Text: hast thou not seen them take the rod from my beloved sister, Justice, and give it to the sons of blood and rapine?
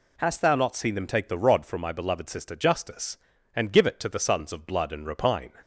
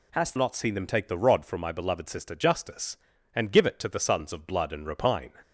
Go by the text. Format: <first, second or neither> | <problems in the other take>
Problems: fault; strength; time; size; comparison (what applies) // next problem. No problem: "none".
first | skips "thou"; at 0.3 s